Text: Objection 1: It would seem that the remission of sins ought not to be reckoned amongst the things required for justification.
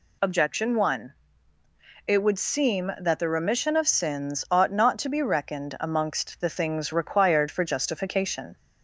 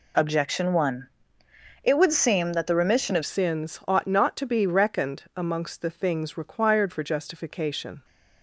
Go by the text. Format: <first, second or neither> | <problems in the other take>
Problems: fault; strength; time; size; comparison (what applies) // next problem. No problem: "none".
first | changes voice at "sins"; from 3.2 s on; 4.8 s long